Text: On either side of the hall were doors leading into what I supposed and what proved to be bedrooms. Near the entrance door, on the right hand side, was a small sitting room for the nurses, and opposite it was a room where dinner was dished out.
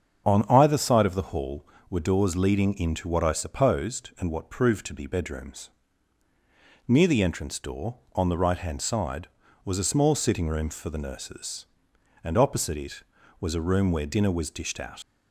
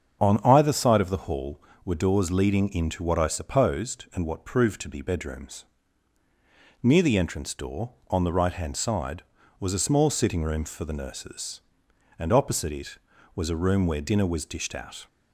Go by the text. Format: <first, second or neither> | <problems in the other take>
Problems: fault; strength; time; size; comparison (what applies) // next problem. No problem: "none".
second | starts louder than the rest; strong; until 1.2 s; 7 dB; strong in the second // leaves "out" unfinished; at 15.0 s; 95 ms